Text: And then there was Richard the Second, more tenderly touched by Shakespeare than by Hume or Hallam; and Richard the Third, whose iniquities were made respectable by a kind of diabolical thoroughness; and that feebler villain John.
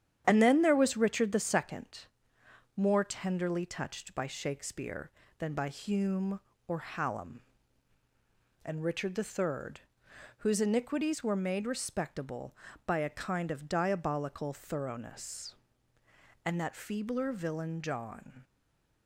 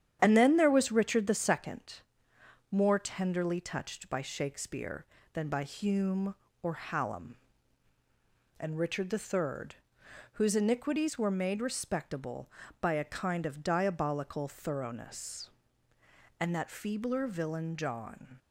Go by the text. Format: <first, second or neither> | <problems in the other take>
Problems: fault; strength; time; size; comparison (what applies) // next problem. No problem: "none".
second | starts louder than the rest; strong; until 1.2 s; 10 dB; strong in the second // stays silent after the last word; slight; from 18.4 s on; 0.6 s long